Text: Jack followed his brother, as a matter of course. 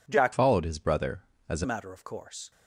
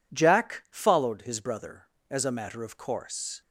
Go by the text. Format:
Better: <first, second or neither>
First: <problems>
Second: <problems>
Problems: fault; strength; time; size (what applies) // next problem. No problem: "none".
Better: second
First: changes voice from "followed" to "a"; from 0.3 to 1.6 s; 1.3 s long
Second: none